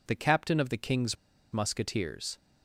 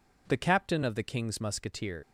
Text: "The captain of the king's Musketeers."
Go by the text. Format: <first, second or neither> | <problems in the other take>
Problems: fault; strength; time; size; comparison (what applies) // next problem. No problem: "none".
second | pauses between "king's" and "Musketeers"; at 1.1 s; 0.38 s long